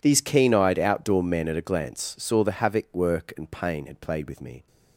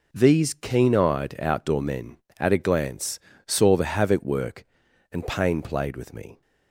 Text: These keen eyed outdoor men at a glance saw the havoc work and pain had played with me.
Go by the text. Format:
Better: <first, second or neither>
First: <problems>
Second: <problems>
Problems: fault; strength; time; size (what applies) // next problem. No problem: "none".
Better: first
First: none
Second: pauses between "glance" and "saw"; slight; at 3.1 s; 0.30 s long // skips "had"; at 5.6 s